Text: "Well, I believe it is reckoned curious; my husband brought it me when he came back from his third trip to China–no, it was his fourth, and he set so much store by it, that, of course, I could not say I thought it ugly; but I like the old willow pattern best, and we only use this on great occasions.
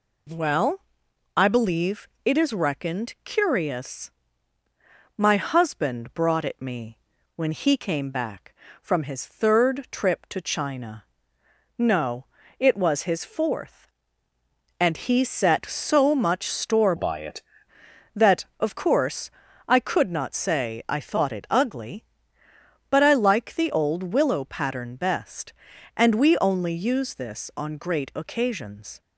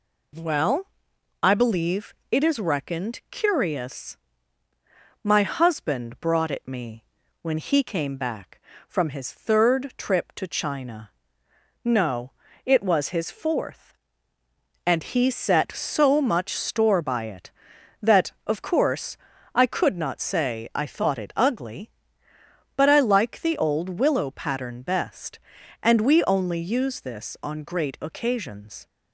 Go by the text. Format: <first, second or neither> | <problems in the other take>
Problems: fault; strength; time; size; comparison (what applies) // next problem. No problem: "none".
second | pauses between "believe" and "it"; slight; at 2.0 s; 0.20 s long; slight in the second // pauses between "me" and "when"; at 6.9 s; 0.38 s long; also in the second // changes voice from "by" to "it"; from 16.9 to 17.4 s; 0.5 s long